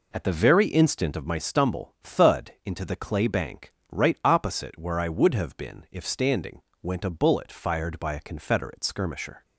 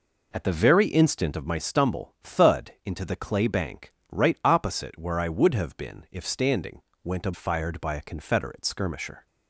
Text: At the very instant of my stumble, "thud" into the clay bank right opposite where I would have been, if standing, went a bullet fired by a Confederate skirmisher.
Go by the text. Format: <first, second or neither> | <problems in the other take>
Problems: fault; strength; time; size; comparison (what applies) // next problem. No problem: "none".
first | pauses between "bank" and "right"; slight; at 3.9 s; 0.18 s long; slight in the first // skips "bullet"; at 7.3 s